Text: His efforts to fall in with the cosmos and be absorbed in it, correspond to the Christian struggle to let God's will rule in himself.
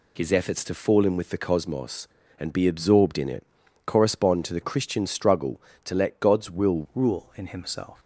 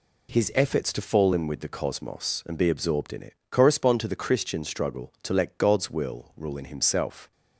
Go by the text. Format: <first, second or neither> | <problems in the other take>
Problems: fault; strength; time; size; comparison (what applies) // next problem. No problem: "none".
second | changes voice at "rule"; from 6.9 s on; 1.0 s long